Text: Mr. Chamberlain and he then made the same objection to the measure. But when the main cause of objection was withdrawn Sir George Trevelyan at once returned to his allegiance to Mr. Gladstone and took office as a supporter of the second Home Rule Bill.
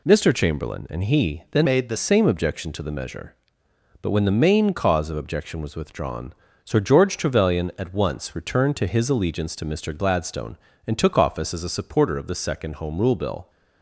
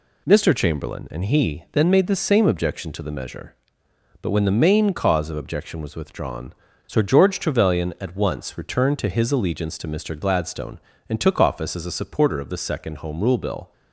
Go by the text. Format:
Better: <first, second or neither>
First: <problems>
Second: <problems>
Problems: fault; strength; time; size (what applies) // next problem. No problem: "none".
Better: second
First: changes voice from "made" to "the"; from 1.6 to 1.9 s; 0.3 s long // pauses between "withdrawn" and "Sir"; slight; at 6.3 s; 0.32 s long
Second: pauses between "withdrawn" and "Sir"; slight; at 6.5 s; 0.35 s long